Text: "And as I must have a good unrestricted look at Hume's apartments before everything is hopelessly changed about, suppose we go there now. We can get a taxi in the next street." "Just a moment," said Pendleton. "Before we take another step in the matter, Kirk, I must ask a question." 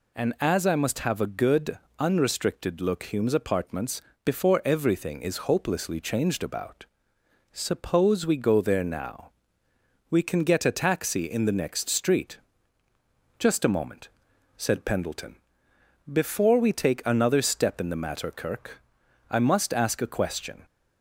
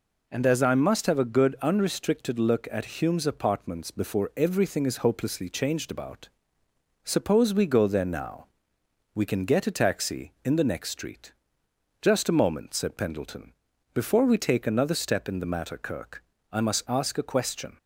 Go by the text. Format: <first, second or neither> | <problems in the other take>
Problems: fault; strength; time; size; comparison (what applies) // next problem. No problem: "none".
second | pauses between "good" and "unrestricted"; slight; at 1.7 s; 0.22 s long // skips "at"; at 3.0 s // pauses between "apartments" and "before"; slight; at 3.9 s; 0.24 s long